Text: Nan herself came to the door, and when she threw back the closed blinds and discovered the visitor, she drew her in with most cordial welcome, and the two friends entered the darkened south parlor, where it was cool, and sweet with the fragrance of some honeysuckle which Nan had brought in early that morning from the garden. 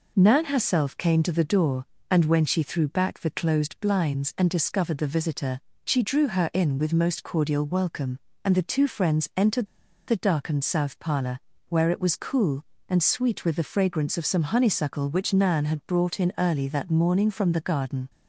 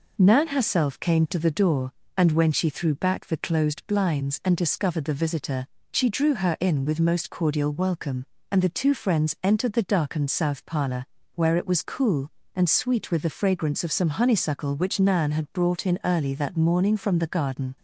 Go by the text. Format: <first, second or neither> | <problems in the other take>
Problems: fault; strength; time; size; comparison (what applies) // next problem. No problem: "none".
second | pauses between "entered" and "the"; at 9.6 s; 0.40 s long